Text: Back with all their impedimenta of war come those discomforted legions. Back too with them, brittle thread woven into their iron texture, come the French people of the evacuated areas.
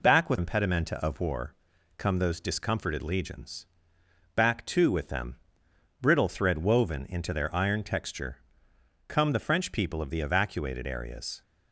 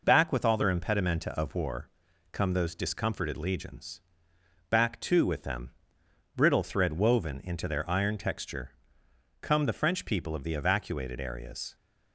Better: second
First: skips "all their"; at 0.3 s // pauses between "war" and "come"; at 1.5 s; 0.44 s long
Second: pauses between "war" and "come"; at 1.8 s; 0.44 s long

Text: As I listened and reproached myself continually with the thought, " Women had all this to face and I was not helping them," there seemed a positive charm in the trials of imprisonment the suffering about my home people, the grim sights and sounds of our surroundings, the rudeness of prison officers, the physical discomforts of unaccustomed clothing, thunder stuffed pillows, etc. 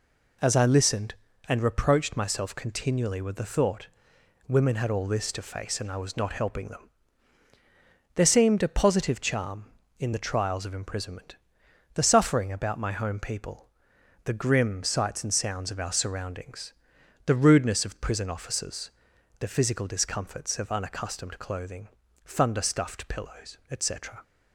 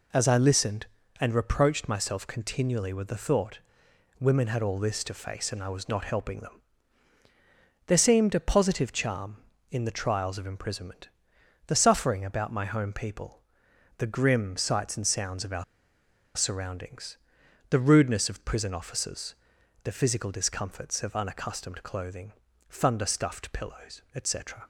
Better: first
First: pauses between "imprisonment" and "the"; noticeable; at 11.3 s; 0.60 s long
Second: pauses between "imprisonment" and "the"; noticeable; at 11.0 s; 0.60 s long // pauses between "our" and "surroundings"; noticeable; at 15.6 s; 0.73 s long

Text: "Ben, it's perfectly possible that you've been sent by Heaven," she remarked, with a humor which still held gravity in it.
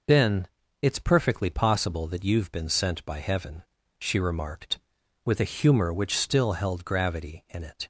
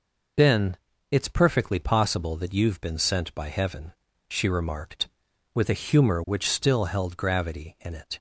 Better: neither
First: none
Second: none

